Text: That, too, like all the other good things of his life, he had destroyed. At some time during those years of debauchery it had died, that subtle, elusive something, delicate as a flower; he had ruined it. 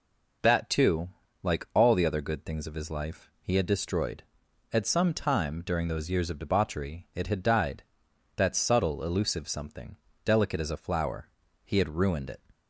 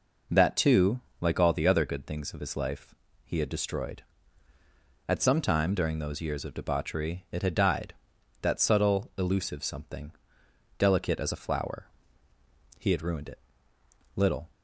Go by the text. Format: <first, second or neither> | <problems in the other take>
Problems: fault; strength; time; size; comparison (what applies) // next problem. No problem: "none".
first | goes on to say "Little"; slight; from 14.1 s on; 0.34 s long